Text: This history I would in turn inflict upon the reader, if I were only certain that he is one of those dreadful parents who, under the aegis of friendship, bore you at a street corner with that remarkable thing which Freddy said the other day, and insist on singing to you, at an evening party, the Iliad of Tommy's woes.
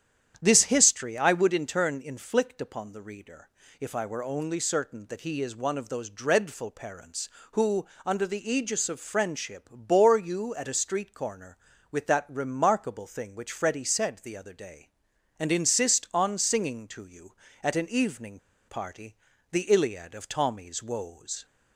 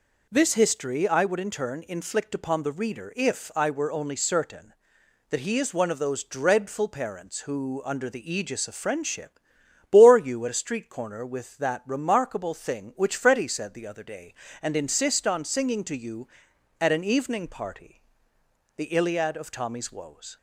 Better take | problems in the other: second | starts louder than the rest; strong; until 1.4 s; 9.5 dB // pauses between "evening" and "party"; slight; at 18.3 s; 0.30 s long

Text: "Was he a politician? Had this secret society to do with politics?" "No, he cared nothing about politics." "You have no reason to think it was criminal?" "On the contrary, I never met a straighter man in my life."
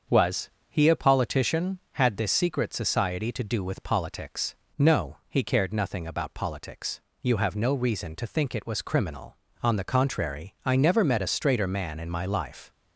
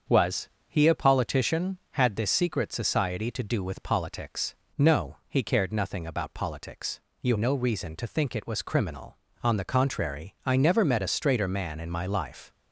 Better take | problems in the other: first | starts louder than the rest; until 1.2 s; 7 dB; also in the first // pauses between "Was" and "he"; slight; at 0.5 s; 0.18 s long; slight in the first // skips "have"; at 7.3 s

